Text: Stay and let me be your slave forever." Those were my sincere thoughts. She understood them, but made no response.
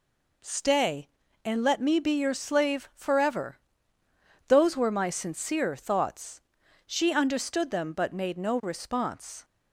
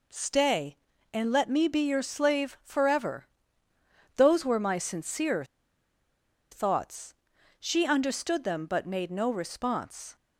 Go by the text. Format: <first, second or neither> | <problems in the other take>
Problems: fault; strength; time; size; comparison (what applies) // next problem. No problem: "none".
first | pauses between "sincere" and "thoughts"; at 5.4 s; 1.0 s long